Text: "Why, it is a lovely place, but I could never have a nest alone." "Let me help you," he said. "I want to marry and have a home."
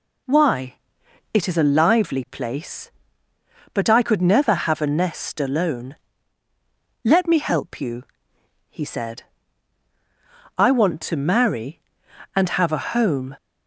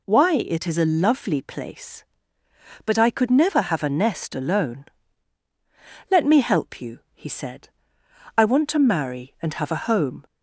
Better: second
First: says "lively" for "lovely"; at 1.6 s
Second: none

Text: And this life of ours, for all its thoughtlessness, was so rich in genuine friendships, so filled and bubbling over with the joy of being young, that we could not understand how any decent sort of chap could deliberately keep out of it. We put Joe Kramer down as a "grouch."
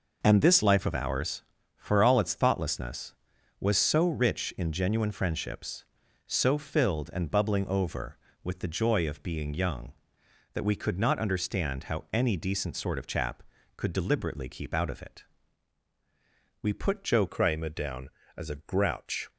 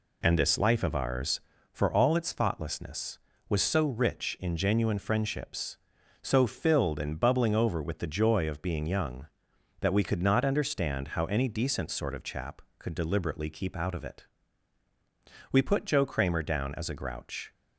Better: second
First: changes voice at "Kramer"; from 17.2 s on; 2.1 s long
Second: none

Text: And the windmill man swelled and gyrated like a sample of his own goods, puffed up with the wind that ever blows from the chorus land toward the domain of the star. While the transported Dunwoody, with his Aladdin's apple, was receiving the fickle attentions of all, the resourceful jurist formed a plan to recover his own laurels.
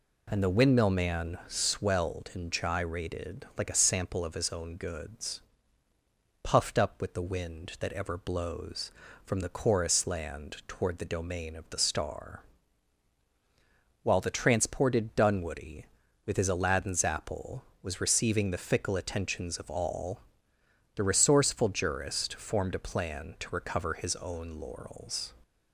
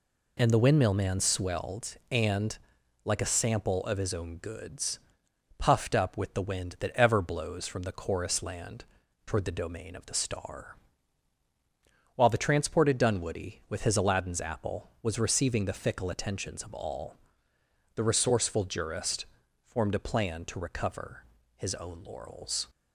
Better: first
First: none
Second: skips "gyrated"; at 2.8 s // pauses between "land" and "toward"; at 8.8 s; 0.42 s long // pauses between "jurist" and "formed"; at 19.2 s; 0.40 s long // pauses between "recover" and "his"; slight; at 21.2 s; 0.32 s long

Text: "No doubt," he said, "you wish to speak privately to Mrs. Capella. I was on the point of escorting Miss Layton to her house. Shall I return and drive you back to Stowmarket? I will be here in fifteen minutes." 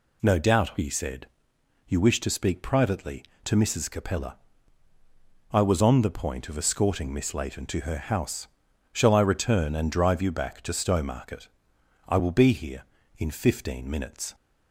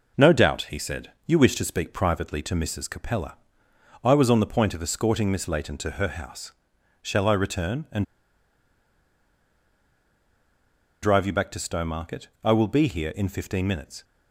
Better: first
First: none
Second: pauses between "and" and "drive"; strong; at 8.0 s; 2.9 s long

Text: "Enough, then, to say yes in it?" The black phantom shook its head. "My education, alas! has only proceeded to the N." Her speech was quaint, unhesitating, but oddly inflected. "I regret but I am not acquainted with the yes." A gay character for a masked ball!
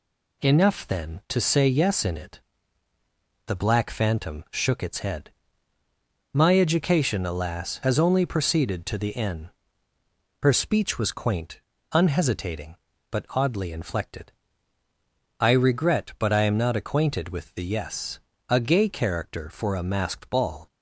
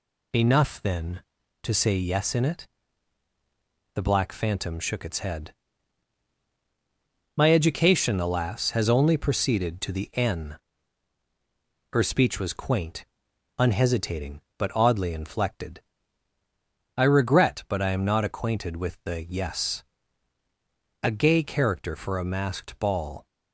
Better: neither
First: none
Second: none

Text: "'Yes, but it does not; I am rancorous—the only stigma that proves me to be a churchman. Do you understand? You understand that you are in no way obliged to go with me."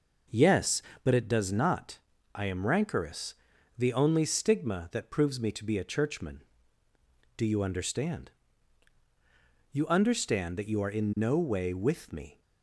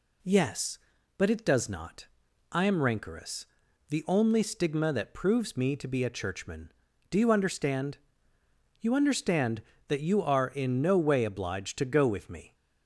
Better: second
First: skips "obliged to go"; at 11.7 s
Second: none

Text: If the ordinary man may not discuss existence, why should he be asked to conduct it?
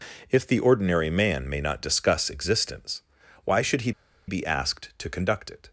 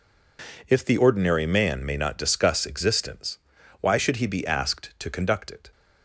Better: second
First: pauses between "he" and "be"; slight; at 3.9 s; 0.35 s long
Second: none

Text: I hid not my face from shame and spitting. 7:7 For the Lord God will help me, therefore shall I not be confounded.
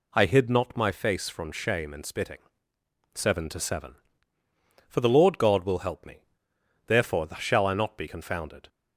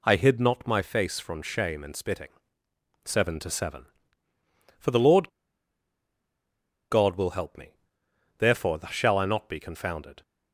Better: first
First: none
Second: pauses between "Lord" and "God"; strong; at 5.2 s; 1.6 s long

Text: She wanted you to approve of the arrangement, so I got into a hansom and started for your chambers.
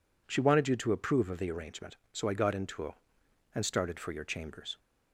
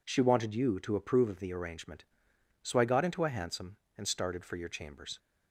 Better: second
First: skips "hansom"; at 3.2 s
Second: none

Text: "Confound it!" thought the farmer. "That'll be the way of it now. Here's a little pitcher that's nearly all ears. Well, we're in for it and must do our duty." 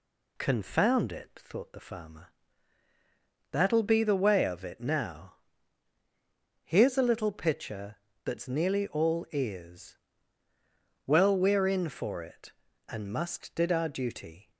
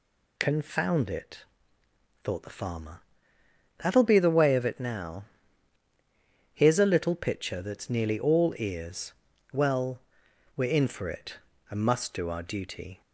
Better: second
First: pauses between "pitcher" and "that's"; slight; at 7.9 s; 0.28 s long // says "did" for "do"; at 13.5 s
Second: none

